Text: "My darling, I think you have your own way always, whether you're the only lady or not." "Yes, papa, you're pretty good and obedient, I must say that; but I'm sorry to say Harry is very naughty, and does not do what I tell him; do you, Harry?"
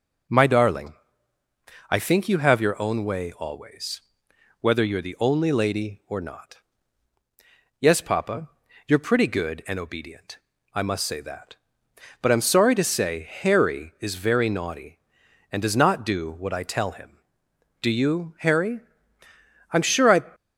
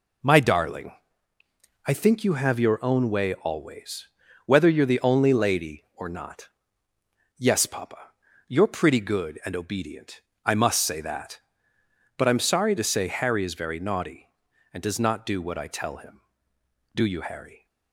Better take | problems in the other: second | goes on to say "I'm sure I"; from 19.7 s on; 0.52 s long

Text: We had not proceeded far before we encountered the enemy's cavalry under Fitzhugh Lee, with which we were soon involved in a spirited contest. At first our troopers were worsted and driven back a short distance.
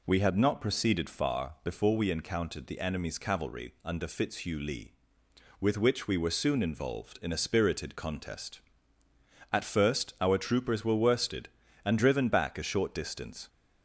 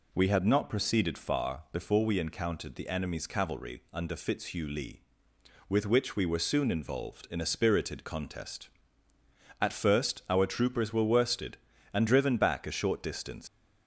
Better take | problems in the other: first | leaves "distance" unfinished; at 13.4 s; 100 ms

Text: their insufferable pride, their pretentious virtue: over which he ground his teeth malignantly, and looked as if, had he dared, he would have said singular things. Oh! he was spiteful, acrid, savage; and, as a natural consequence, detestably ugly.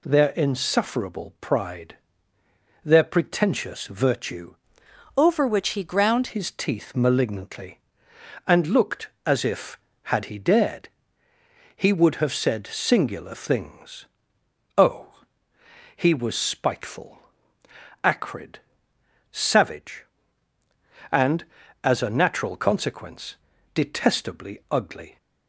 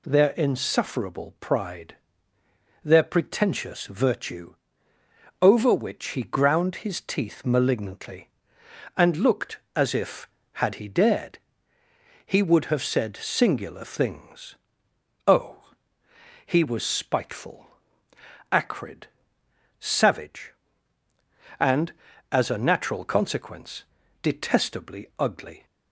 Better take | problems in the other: second | changes voice from "over" to "ground"; from 5.1 to 6.2 s; 1.1 s long

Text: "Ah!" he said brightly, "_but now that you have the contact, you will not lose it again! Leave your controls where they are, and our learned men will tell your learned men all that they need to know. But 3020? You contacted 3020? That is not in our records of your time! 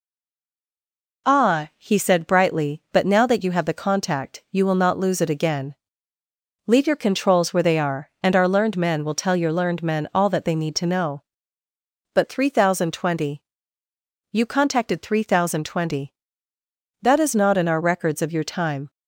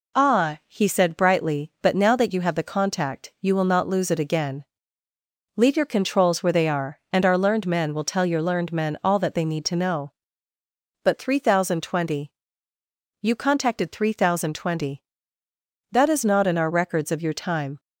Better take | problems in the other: second | stays silent before the first word; noticeable; until 1.2 s; 1.2 s long

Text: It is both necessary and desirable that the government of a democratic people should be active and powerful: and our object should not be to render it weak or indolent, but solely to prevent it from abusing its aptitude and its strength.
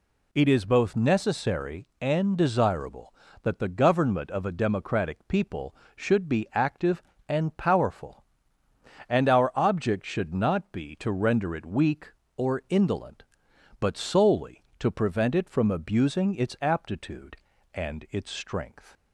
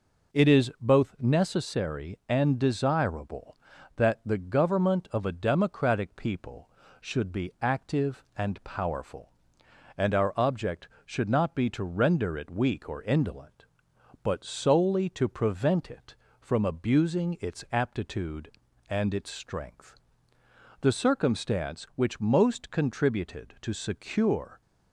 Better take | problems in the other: first | goes on to say "The circumstance which most contributed to secure"; strong; from 20.8 s on; 3.8 s long

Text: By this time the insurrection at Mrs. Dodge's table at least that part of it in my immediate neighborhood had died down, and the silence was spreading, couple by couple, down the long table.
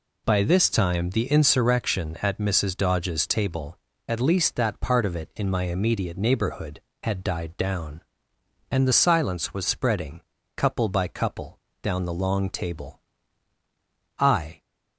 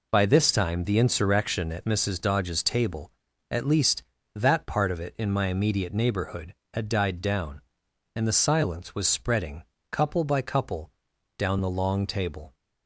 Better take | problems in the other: second | goes on to say "I"; slight; from 14.1 s on; 0.40 s long

